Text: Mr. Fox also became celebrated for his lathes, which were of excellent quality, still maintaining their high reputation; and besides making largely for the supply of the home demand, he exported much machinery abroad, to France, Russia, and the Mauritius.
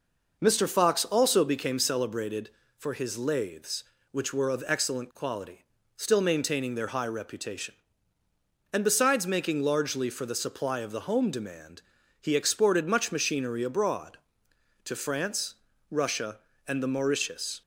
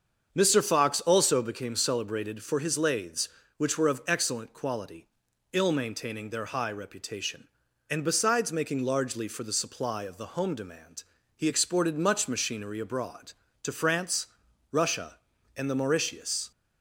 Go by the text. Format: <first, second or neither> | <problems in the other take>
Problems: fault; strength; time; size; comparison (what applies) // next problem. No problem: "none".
first | starts louder than the rest; until 1.3 s; 7 dB // says "ill" for "still"; at 5.5 s